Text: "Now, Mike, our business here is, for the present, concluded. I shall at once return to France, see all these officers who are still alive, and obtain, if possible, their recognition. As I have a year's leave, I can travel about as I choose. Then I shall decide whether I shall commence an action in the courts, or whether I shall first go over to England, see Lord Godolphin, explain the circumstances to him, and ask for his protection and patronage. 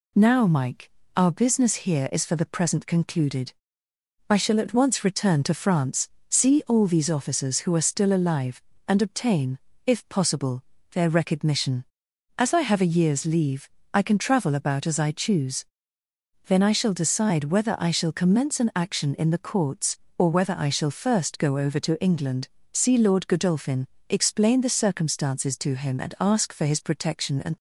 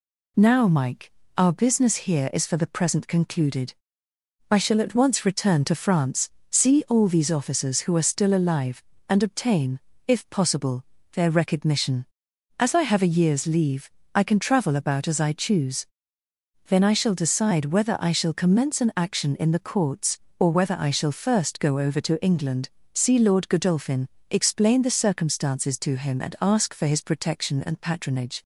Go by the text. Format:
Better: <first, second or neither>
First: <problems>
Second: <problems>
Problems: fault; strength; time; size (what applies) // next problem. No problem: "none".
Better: second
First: stops before "patronage"; at 27.5 s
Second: none